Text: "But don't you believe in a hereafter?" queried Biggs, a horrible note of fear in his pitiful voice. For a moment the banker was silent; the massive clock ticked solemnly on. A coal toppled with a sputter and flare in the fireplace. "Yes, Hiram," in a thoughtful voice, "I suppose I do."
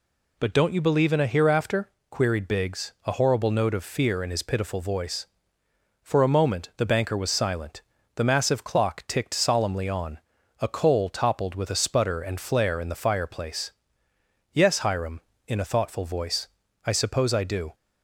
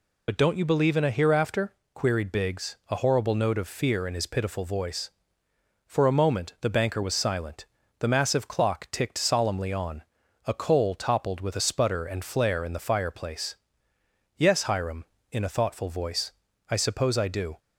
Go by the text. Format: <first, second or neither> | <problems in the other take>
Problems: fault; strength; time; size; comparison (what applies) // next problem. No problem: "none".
first | loses the start of "But"; at 0.2 s; 55 ms